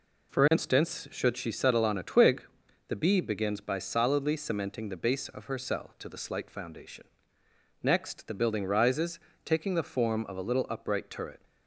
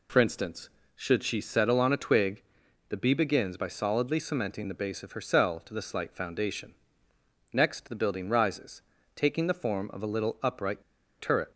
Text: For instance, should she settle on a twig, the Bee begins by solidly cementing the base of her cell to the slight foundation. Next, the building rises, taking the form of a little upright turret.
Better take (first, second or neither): first